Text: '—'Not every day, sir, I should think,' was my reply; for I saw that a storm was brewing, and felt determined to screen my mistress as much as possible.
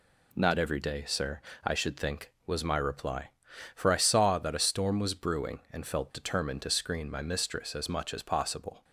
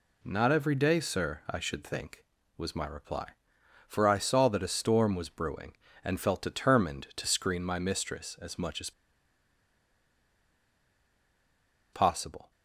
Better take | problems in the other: first | pauses between "as" and "possible"; strong; at 8.9 s; 3.0 s long

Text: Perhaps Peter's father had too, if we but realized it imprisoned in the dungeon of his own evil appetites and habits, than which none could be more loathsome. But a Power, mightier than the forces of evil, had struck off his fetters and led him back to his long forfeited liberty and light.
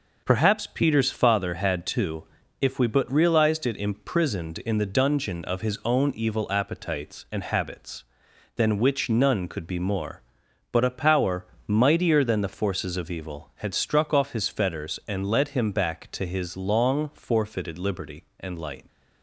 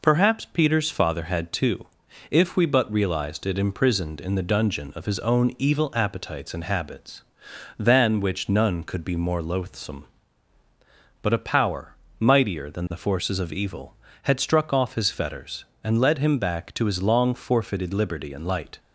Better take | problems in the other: second | skips "loathsome"; at 10.4 s

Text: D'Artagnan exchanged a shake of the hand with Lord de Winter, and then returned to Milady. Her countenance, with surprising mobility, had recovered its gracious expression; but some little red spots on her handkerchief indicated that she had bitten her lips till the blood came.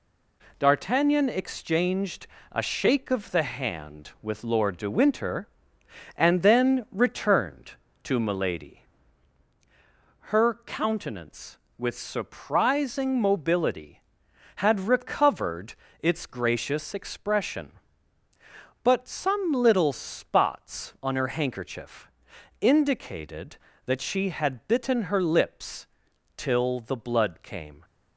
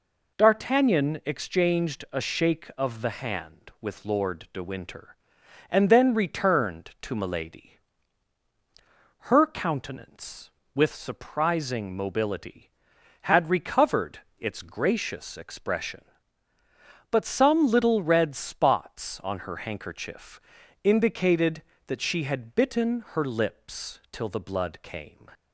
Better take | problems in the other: second | pauses between "exchanged" and "a"; slight; at 2.2 s; 0.26 s long // pauses between "recovered" and "its"; slight; at 15.7 s; 0.26 s long; slight in the second // skips "red"; at 19.9 s // pauses between "handkerchief" and "indicated"; noticeable; at 22.1 s; 0.50 s long; also in the second // pauses between "lips" and "till"; noticeable; at 25.8 s; 0.50 s long

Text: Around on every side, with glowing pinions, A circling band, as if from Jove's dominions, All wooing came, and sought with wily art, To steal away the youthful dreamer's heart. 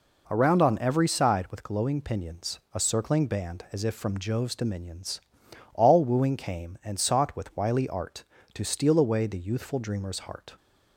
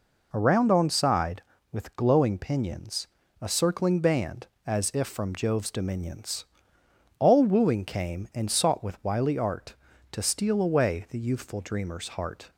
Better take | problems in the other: first | skips "every"; at 0.8 s

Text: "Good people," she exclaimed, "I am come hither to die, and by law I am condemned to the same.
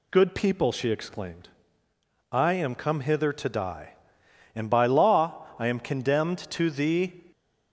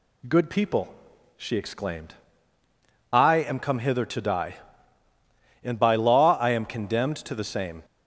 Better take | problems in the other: second | stops before "same"; at 7.3 s

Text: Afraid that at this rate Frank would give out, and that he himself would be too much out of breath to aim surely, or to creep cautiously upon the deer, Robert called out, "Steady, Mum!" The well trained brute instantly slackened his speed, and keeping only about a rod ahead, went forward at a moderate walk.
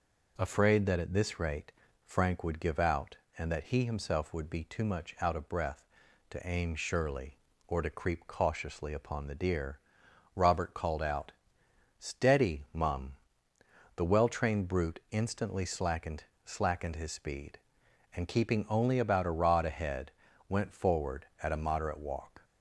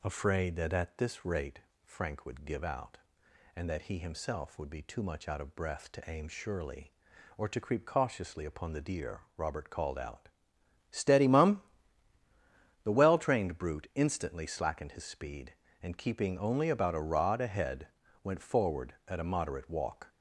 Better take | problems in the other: second | pauses between "rate" and "Frank"; slight; at 1.7 s; 0.34 s long; slight in the second // says "slackened" twice; at 16.4 s

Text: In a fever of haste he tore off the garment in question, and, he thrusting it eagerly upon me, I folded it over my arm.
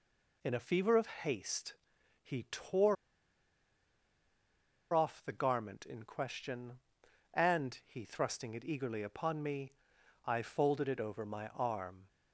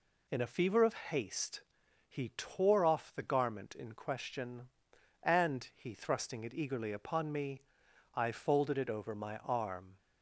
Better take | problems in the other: second | pauses between "haste" and "he"; noticeable; at 1.7 s; 0.48 s long; noticeable in the second // pauses between "tore" and "off"; strong; at 2.9 s; 1.9 s long

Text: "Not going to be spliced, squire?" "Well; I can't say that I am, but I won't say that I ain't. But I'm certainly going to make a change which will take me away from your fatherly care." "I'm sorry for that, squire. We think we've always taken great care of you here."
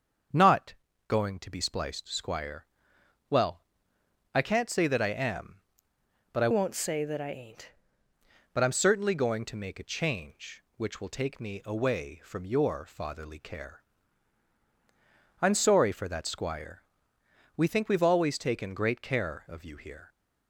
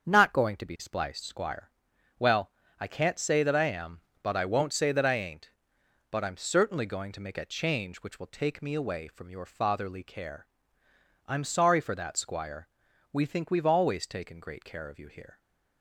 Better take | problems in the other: second | starts louder than the rest; until 1.6 s; 7 dB; also in the second // pauses between "Not" and "going"; slight; at 0.7 s; 0.34 s long // changes voice from "won't" to "ain't"; from 6.5 to 7.7 s; 1.2 s long

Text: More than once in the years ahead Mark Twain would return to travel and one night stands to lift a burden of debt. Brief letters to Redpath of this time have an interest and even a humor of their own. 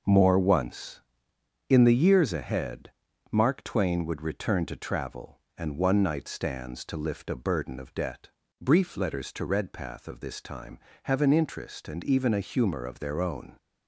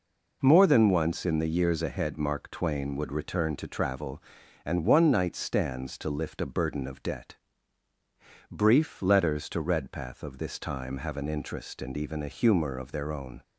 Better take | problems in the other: second | skips "than"; at 0.3 s // pauses between "ahead" and "Mark"; at 2.9 s; 0.40 s long

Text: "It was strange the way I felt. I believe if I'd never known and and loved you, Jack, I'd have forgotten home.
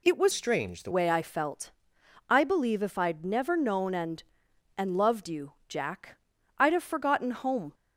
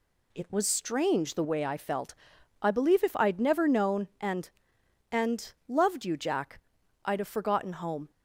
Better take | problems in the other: second | changes voice from "strange" to "the"; from 0.3 to 0.9 s; 0.6 s long

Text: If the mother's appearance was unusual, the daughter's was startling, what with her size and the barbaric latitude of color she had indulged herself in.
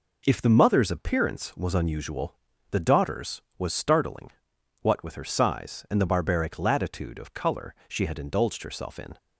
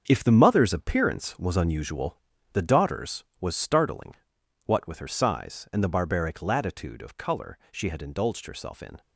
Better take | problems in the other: first | gets quieter; strong; throughout; 9.5 dB

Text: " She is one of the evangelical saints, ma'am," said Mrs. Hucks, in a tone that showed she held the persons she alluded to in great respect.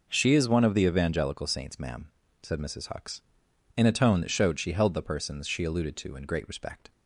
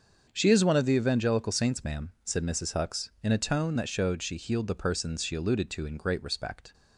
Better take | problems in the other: first | starts louder than the rest; until 1.3 s; 7 dB // says "healed" for "held"; at 4.3 s

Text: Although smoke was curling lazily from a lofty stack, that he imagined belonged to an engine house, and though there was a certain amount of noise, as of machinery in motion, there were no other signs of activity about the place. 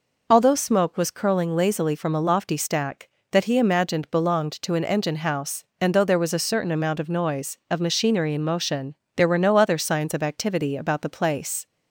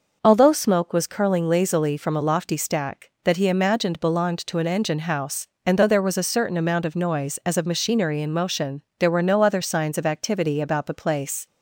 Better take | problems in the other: second | skips "as"; at 7.6 s

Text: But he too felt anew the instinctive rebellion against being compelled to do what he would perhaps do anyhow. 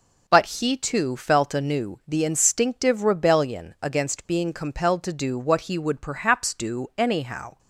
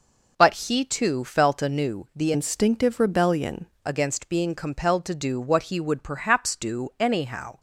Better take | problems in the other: first | starts louder than the rest; noticeable; until 1.5 s; 6 dB; also in the first // changes voice from "instinctive" to "rebellion"; from 2.3 to 3.6 s; 1.3 s long

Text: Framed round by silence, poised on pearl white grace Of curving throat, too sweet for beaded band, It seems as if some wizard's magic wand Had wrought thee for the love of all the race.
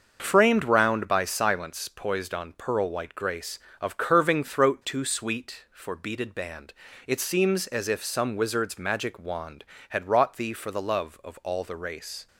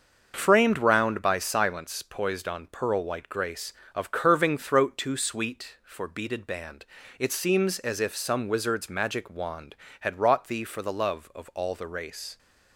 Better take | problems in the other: neither | starts louder than the rest; the same in both

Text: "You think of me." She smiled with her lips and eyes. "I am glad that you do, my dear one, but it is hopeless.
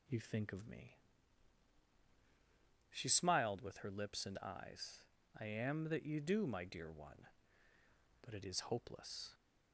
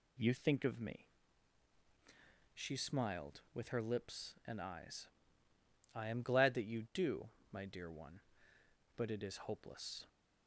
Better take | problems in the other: second | skips "glad"; at 5.8 s

